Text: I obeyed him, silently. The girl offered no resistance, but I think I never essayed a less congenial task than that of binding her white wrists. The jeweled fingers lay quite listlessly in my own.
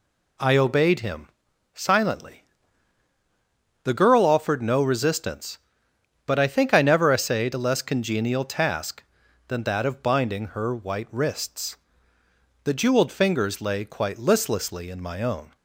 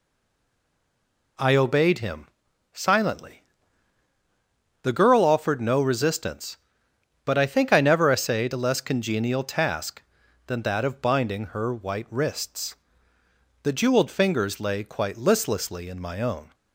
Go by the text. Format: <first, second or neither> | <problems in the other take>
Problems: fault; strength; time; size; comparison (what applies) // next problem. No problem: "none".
first | stays silent before the first word; noticeable; until 1.3 s; 1.3 s long